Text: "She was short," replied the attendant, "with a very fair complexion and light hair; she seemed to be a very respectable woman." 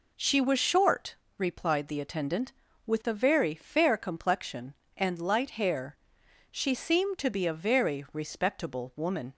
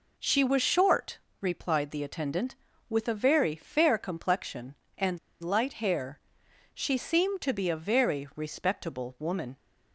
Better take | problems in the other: first | pauses between "and" and "light"; slight; at 5.1 s; 0.24 s long

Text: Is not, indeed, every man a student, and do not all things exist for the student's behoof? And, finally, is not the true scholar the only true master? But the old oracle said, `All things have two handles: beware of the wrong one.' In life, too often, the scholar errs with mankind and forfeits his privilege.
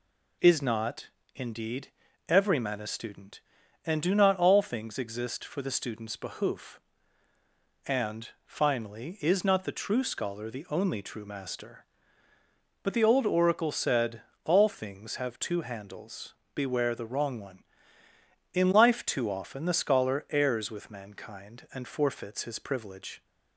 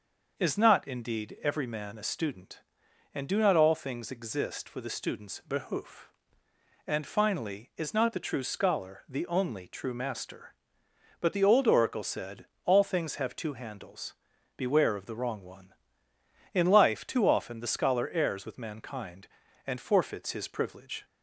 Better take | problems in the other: second | skips "of"; at 16.9 s

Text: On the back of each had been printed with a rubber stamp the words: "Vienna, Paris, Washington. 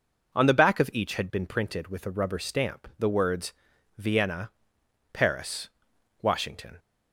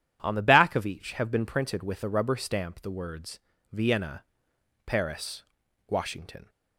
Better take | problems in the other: first | says "have" for "had"; at 1.1 s

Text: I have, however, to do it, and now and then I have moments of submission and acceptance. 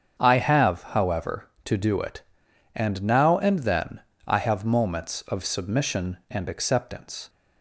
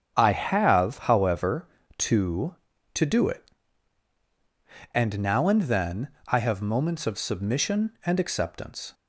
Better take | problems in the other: first | starts louder than the rest; strong; until 1.1 s; 8 dB; strong in the first // says "to" twice; at 2.9 s // pauses between "then" and "I"; slight; at 6.0 s; 0.18 s long; slight in the first

